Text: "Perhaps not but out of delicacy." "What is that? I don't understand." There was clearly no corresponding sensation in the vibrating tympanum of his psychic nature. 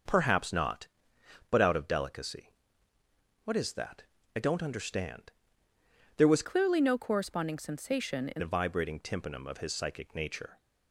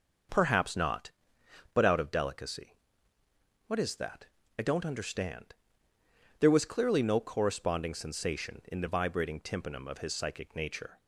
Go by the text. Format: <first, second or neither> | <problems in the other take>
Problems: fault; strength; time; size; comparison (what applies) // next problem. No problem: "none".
second | starts louder than the rest; noticeable; until 1.7 s; 6 dB; also in the second // changes voice from "clearly" to "in"; from 6.4 to 8.4 s; 2.0 s long